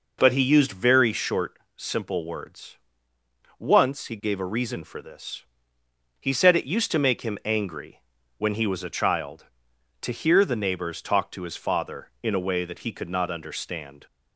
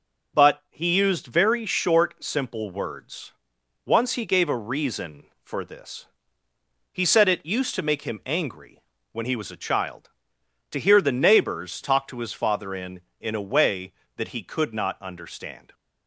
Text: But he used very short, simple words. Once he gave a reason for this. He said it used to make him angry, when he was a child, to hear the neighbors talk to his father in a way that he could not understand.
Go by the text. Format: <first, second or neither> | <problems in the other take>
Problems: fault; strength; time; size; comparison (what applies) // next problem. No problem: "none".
first | says "in" twice; at 13.1 s